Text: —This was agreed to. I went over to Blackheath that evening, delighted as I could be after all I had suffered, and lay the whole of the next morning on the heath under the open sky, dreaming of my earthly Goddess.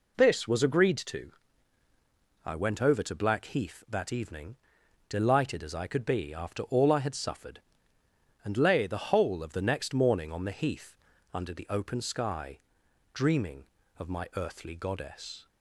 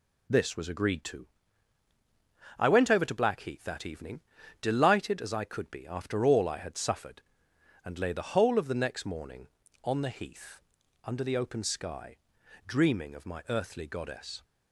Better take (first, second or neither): neither